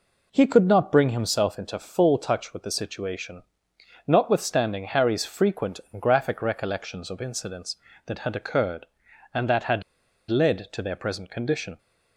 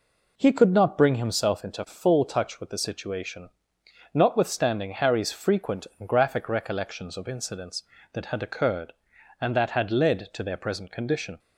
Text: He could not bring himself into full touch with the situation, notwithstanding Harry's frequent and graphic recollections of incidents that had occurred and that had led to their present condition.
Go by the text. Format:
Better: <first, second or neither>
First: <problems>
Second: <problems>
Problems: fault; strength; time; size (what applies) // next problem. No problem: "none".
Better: second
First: pauses between "had" and "led"; noticeable; at 9.8 s; 0.46 s long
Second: none